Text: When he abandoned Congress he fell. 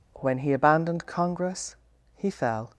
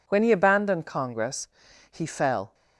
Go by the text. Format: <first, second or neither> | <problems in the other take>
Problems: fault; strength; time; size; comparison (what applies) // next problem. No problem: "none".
neither | pauses between "Congress" and "he"; the same in both